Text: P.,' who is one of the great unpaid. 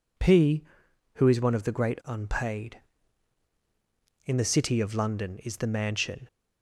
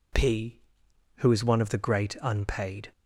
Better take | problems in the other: second | goes on to say "In the City of London is the Mansion"; strong; from 4.2 s on; 2.0 s long

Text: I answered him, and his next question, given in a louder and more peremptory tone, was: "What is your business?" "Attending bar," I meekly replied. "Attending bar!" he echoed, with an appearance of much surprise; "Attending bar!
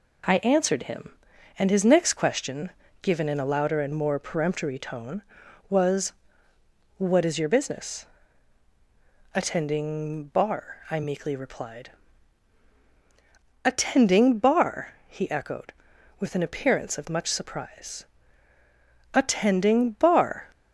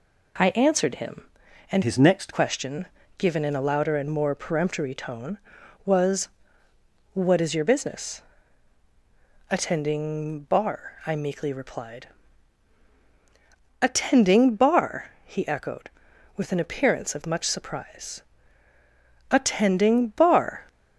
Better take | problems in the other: first | changes voice from "his" to "next"; from 1.8 to 2.3 s; 0.5 s long

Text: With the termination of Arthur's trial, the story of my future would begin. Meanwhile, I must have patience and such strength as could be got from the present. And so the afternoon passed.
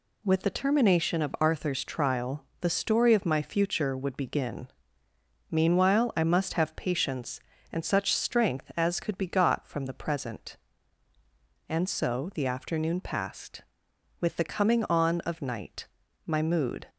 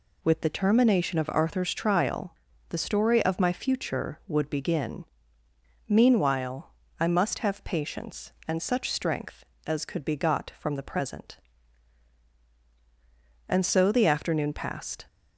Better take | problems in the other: second | goes on to say "With the coming on of night my mood"; strong; from 14.2 s on; 2.6 s long

